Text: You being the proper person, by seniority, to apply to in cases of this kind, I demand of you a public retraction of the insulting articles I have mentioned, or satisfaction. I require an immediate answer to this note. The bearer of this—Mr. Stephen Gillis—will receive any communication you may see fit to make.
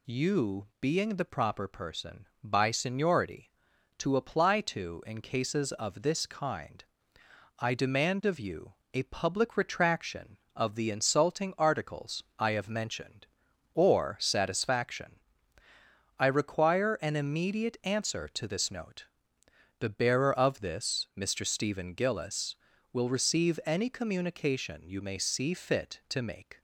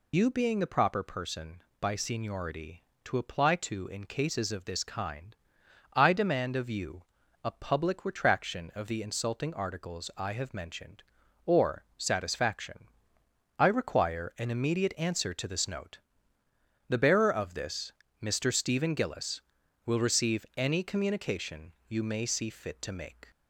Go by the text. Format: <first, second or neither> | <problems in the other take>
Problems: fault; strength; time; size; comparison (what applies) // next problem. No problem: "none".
first | loses the start of "You"; at 0.1 s; 45 ms // pauses between "you" and "a"; at 7.0 s; 0.40 s long; slight in the first // pauses between "or" and "satisfaction"; slight; at 11.8 s; 0.16 s long // pauses between "communication" and "you"; slight; at 21.7 s; 0.16 s long